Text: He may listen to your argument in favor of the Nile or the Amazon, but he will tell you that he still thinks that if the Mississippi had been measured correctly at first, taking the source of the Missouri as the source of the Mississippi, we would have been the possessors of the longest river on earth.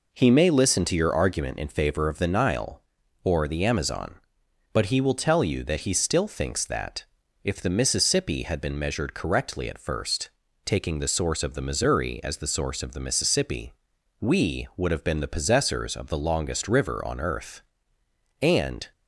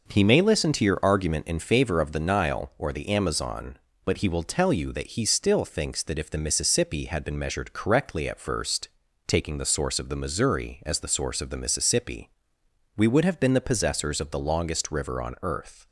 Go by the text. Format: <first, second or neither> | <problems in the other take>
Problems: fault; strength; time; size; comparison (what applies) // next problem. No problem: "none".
second | pauses between "that" and "if"; at 7.0 s; 0.38 s long // goes on to say "And"; from 18.4 s on; 0.50 s long